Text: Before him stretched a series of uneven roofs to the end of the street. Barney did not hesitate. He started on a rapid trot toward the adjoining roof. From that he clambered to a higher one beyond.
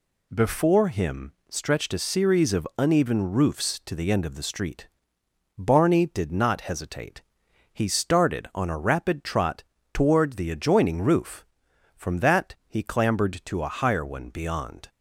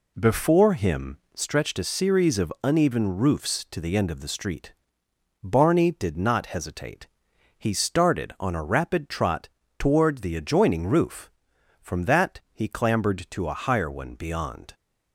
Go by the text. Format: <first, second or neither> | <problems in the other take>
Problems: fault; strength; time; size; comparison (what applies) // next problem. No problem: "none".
first | starts louder than the rest; slight; until 1.6 s; 2.5 dB // pauses between "him" and "stretched"; slight; at 1.1 s; 0.16 s long; slight in the first // pauses between "trot" and "toward"; slight; at 9.4 s; 0.30 s long; slight in the first